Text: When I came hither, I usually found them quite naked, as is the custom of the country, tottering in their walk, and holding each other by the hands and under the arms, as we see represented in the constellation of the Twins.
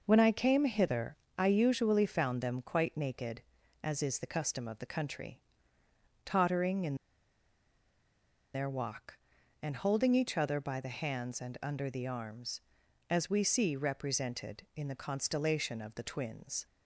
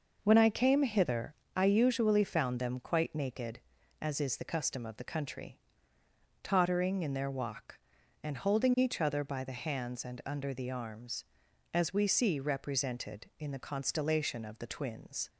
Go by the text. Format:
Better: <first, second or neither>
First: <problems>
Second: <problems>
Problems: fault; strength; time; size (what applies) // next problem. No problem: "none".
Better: second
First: pauses between "in" and "their"; strong; at 6.9 s; 1.5 s long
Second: none